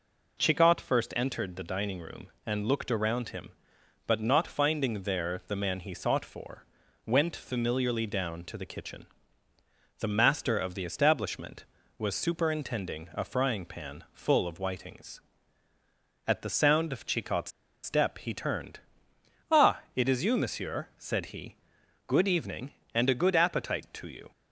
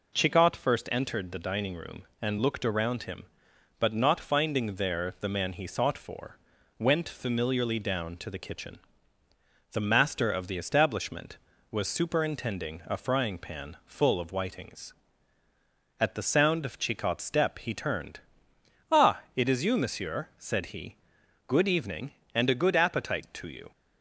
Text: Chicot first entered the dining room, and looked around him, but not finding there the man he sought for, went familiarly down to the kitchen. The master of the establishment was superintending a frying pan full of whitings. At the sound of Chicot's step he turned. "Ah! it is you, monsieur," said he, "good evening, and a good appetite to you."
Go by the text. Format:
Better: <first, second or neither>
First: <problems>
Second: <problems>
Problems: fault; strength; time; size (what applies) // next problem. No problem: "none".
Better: second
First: pauses between "Chicot's" and "step"; slight; at 17.5 s; 0.33 s long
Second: none